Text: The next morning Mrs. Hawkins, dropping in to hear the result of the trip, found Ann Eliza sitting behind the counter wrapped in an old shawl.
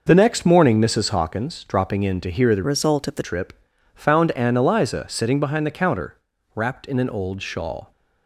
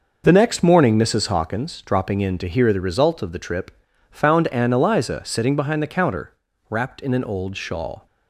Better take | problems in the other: second | changes voice from "result" to "the"; from 2.6 to 3.2 s; 0.6 s long // pauses between "counter" and "wrapped"; at 6.1 s; 0.40 s long; also in the second

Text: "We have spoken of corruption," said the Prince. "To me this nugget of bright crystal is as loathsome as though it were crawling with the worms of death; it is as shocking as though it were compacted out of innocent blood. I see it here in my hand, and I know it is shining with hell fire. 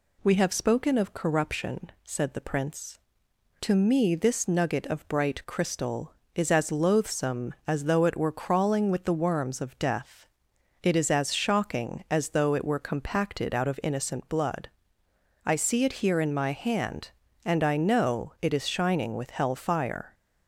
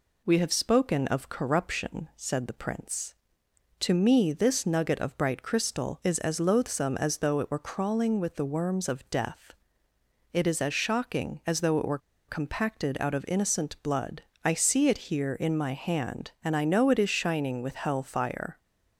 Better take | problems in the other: first | pauses between "were" and "compacted"; slight; at 11.9 s; 0.29 s long

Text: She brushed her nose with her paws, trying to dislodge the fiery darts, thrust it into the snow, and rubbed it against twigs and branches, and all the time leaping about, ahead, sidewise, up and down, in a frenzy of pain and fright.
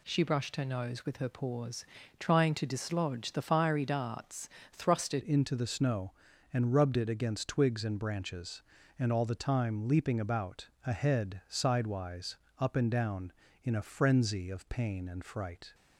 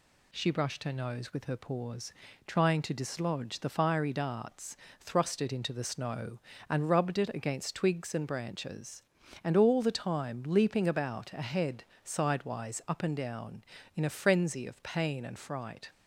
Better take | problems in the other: second | changes voice at "into"; from 5.2 s on; 10.5 s long

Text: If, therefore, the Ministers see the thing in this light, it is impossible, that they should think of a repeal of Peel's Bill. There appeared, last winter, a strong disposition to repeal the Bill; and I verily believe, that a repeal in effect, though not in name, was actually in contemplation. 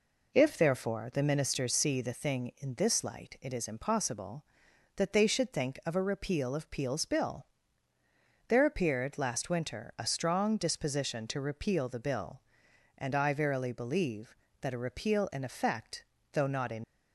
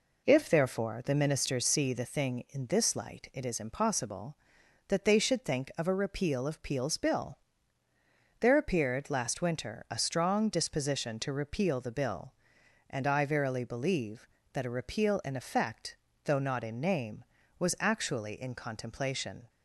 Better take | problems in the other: second | stops before "name was actually in contemplation"; at 16.8 s

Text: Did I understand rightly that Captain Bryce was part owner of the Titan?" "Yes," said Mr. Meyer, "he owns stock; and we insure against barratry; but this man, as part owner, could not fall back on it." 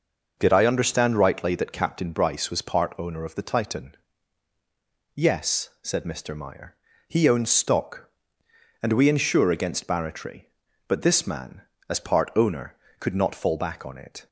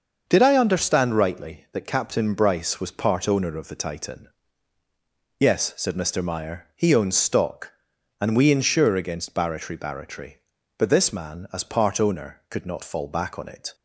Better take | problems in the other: first | starts louder than the rest; until 1.2 s; 6.5 dB // says "barratry" twice; at 9.7 s

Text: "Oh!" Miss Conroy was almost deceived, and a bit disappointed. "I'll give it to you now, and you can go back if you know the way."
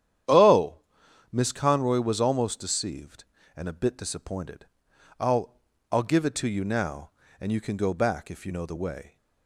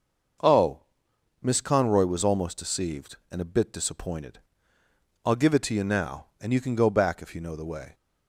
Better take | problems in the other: second | starts louder than the rest; strong; until 1.8 s; 10 dB; noticeable in the second // says "I'll" twice; at 5.9 s

